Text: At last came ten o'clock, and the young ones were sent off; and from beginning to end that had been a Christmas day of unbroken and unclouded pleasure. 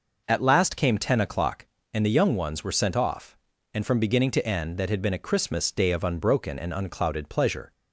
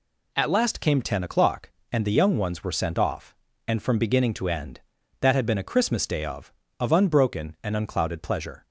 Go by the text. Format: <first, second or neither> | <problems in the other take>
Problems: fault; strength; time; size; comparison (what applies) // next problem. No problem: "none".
first | says "of" twice; at 6.7 s